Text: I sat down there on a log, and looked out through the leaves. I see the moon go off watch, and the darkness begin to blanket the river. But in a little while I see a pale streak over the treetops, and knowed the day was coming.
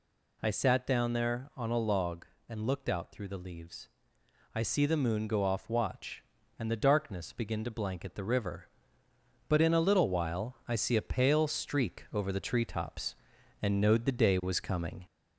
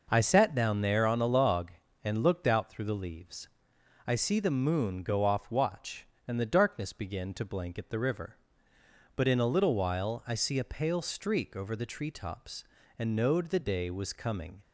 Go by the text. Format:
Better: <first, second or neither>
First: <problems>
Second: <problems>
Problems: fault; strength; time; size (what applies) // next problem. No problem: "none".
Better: second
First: gets louder; slight; throughout; 2 dB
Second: none